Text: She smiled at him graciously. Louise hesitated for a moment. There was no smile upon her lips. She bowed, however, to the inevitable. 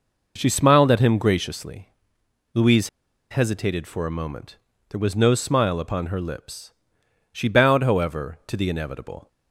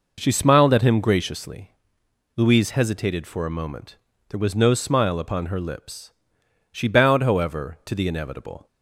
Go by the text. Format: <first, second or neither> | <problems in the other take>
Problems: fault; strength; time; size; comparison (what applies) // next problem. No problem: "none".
second | pauses between "Louise" and "hesitated"; at 2.8 s; 0.42 s long